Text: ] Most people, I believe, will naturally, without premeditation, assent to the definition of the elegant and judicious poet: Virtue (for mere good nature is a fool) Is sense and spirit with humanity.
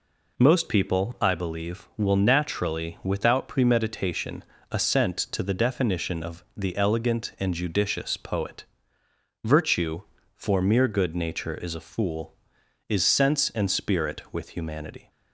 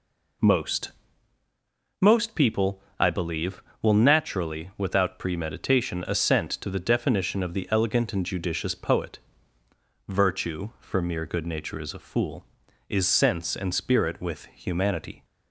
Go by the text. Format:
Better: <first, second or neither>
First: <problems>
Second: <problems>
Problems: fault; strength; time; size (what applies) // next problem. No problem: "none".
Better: first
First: none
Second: says "Most" twice; at 2.0 s